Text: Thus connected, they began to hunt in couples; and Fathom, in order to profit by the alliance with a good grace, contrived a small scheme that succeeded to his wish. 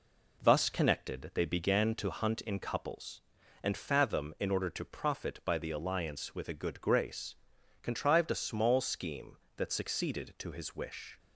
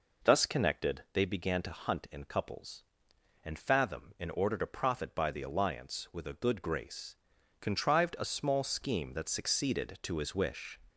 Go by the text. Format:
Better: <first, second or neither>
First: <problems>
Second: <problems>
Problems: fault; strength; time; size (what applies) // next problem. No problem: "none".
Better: neither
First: none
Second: none